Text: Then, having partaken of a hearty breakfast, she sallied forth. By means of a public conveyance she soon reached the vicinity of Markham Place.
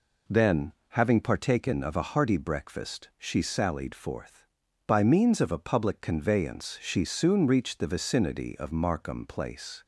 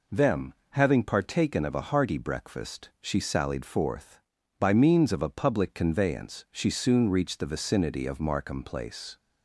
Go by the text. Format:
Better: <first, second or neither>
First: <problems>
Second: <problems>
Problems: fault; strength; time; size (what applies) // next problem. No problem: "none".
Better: first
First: none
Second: says "Them" for "Then"; at 0.1 s